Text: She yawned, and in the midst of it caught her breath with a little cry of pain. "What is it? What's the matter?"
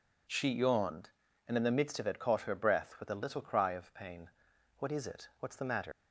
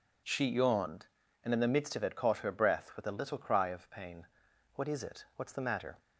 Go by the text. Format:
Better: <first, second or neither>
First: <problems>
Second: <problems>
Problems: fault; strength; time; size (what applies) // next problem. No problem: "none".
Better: second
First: leaves "matter" unfinished; at 5.9 s; 105 ms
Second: none